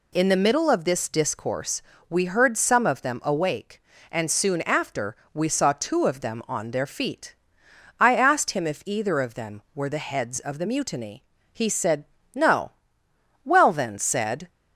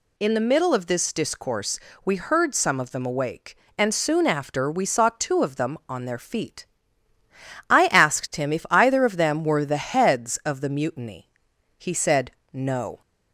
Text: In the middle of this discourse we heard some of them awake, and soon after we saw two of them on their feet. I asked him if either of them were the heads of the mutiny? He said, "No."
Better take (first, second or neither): second